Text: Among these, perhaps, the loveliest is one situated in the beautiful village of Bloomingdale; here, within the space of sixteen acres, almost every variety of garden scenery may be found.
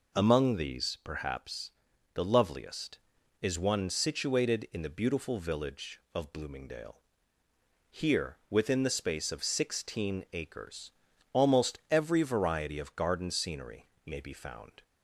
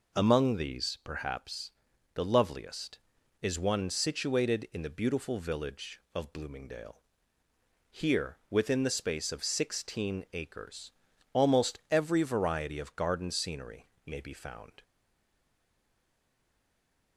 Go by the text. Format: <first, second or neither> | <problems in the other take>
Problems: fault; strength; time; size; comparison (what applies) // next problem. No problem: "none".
first | pauses between "scenery" and "may"; slight; at 13.8 s; 0.16 s long; slight in the first // stays silent after the last word; from 14.8 s on; 2.3 s long